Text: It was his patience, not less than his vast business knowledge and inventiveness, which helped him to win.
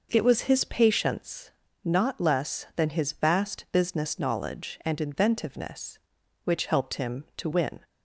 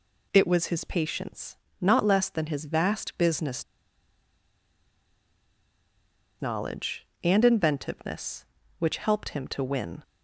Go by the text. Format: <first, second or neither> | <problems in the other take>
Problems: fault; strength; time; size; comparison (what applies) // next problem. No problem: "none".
first | pauses between "business" and "knowledge"; strong; at 3.6 s; 2.7 s long